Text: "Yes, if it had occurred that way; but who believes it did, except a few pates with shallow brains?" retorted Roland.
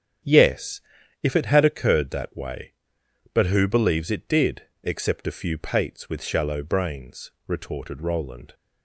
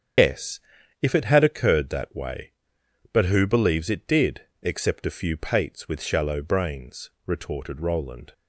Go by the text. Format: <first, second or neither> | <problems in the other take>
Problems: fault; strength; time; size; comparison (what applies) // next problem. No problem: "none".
first | loses the start of "Yes"; at 0.1 s; 155 ms // starts louder than the rest; strong; until 1.6 s; 8 dB; strong in the first